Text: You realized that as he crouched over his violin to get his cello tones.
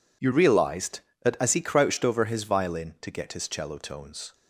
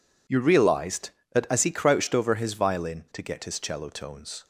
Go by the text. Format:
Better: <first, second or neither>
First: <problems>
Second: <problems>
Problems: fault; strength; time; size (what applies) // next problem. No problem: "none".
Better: neither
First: none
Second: none